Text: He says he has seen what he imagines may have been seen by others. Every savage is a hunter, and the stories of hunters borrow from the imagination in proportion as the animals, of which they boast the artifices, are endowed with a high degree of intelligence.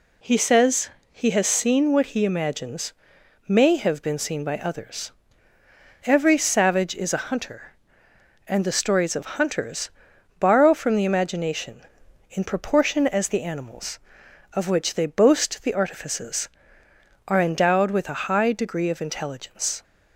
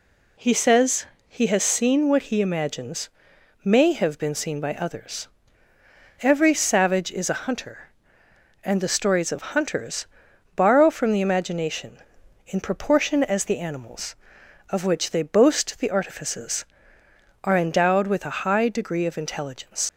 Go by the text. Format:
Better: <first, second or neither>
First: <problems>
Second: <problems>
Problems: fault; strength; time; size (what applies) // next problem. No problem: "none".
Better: first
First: pauses between "says" and "he"; slight; at 0.9 s; 0.20 s long // pauses between "imagines" and "may"; noticeable; at 2.9 s; 0.56 s long // pauses between "of" and "hunters"; slight; at 9.2 s; 0.16 s long // pauses between "hunters" and "borrow"; noticeable; at 9.8 s; 0.50 s long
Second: pauses between "says" and "he"; slight; at 1.0 s; 0.20 s long // pauses between "imagines" and "may"; noticeable; at 3.0 s; 0.56 s long // pauses between "of" and "hunters"; slight; at 9.4 s; 0.16 s long // pauses between "hunters" and "borrow"; noticeable; at 10.0 s; 0.50 s long // leaves "intelligence" unfinished; at 19.8 s; 95 ms